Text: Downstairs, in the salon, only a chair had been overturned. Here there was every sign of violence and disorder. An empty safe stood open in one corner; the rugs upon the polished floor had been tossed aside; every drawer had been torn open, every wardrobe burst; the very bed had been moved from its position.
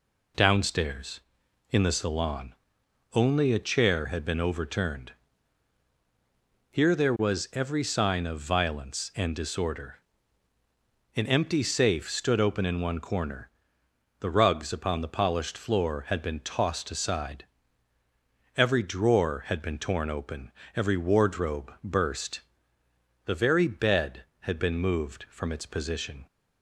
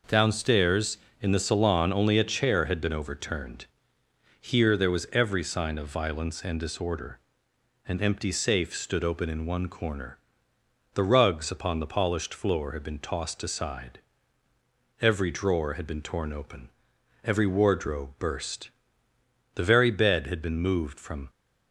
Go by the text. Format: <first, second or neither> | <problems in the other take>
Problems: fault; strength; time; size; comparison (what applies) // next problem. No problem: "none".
first | stops before "its position"; at 21.2 s